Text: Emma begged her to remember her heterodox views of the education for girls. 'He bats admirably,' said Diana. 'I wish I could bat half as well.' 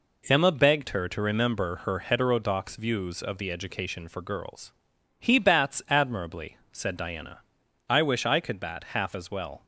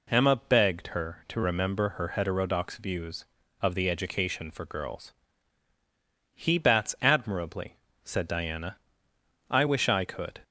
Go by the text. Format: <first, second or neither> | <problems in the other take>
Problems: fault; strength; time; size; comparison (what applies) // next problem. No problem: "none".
first | stops before "bat half as well"; at 10.4 s